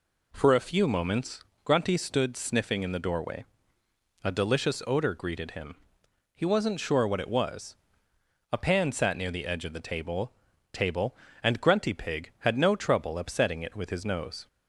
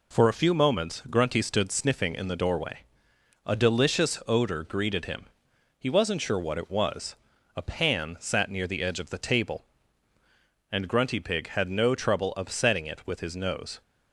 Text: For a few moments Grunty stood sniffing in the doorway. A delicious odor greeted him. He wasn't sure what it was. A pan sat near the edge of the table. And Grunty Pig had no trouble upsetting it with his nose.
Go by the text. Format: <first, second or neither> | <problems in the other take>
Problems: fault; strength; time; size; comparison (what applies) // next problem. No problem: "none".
second | pauses between "moments" and "Grunty"; slight; at 1.4 s; 0.22 s long // says "table" twice; at 10.7 s